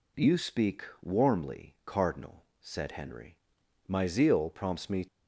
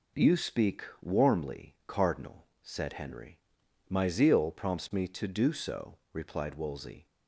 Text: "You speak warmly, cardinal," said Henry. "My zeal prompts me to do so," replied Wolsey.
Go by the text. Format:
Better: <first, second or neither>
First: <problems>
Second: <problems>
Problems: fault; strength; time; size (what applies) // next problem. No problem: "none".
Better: second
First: pauses between "speak" and "warmly"; slight; at 0.8 s; 0.18 s long // stops before "to do so replied Wolsey"; at 5.0 s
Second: pauses between "speak" and "warmly"; slight; at 0.8 s; 0.18 s long